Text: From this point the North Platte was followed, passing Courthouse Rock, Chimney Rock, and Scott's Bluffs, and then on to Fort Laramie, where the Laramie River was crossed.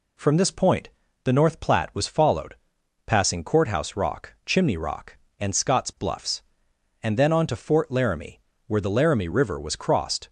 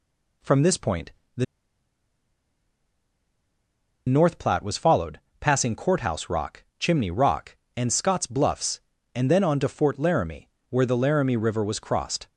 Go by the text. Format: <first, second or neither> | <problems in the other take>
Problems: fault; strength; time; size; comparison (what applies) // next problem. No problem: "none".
first | pauses between "point" and "the"; slight; at 1.1 s; 0.24 s long; slight in the first // pauses between "the" and "North"; strong; at 1.4 s; 2.6 s long